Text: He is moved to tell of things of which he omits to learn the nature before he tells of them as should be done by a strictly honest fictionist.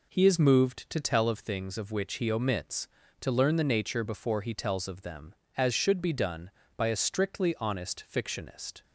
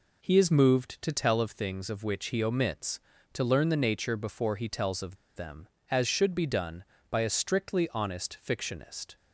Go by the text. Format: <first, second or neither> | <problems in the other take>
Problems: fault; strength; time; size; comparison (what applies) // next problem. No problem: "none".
first | pauses between "of" and "them"; slight; at 5.1 s; 0.19 s long